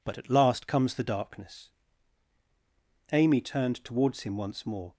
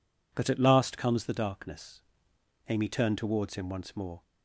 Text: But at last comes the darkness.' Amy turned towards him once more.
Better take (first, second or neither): neither